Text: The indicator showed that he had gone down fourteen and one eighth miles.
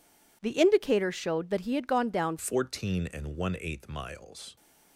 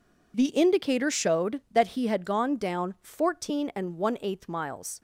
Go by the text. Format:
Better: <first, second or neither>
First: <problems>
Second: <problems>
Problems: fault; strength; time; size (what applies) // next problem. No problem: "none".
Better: second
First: changes voice at "fourteen"; from 2.3 s on; 2.2 s long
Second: none